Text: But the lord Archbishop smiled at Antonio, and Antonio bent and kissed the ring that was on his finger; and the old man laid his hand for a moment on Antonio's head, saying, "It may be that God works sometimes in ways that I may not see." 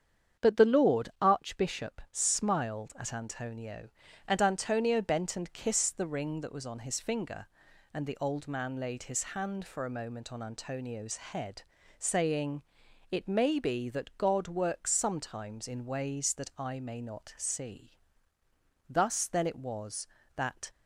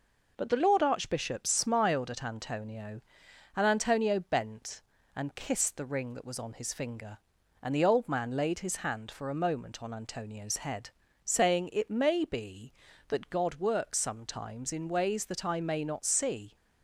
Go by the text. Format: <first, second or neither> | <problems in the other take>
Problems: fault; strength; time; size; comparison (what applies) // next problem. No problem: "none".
second | starts louder than the rest; strong; until 1.5 s; 8 dB // goes on to say "Thus then it was that"; strong; from 18.8 s on; 1.8 s long